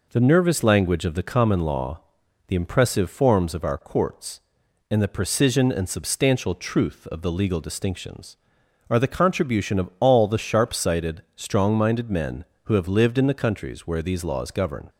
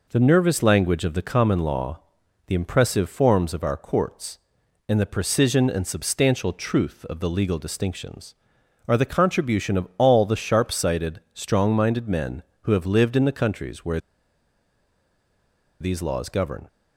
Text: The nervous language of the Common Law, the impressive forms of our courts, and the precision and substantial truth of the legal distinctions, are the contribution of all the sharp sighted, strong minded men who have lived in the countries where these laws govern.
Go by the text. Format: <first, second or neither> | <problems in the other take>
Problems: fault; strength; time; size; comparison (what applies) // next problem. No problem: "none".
first | pauses between "where" and "these"; strong; at 13.9 s; 1.8 s long